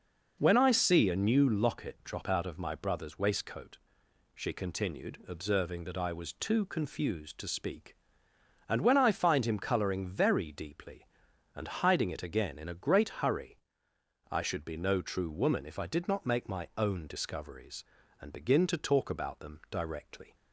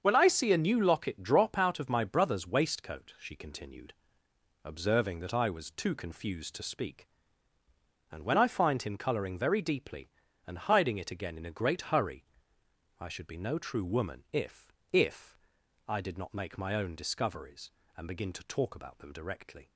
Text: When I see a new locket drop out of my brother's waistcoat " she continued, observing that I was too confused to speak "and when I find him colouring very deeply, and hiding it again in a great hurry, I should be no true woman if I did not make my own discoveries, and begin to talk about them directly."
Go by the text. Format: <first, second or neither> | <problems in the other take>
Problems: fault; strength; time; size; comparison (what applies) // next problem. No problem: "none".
first | starts louder than the rest; until 1.0 s; 7 dB // says "if" twice; at 14.9 s